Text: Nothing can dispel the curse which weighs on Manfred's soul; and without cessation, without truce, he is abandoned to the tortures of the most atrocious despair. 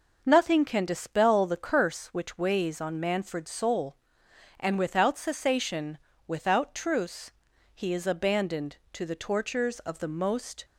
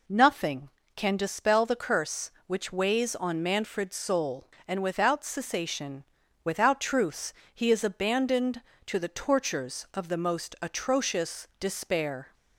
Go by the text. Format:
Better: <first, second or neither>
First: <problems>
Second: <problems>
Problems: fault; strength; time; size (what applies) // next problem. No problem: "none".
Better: second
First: stops before "atrocious despair"; at 10.6 s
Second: none